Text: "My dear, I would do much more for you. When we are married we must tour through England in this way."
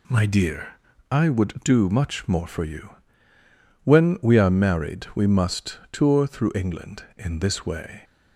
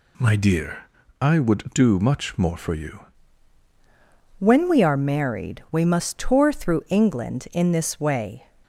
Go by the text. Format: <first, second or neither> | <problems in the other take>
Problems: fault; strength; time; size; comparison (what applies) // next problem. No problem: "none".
first | changes voice at "When"; from 4.3 s on; 4.1 s long